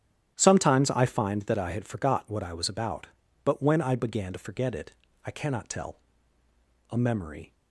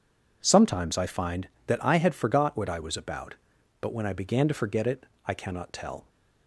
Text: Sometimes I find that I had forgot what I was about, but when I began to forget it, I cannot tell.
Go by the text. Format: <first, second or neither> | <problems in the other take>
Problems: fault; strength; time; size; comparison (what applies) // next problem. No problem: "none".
second | starts louder than the rest; strong; until 1.3 s; 10.5 dB // goes on to say "A memory"; noticeable; from 6.8 s on; 0.64 s long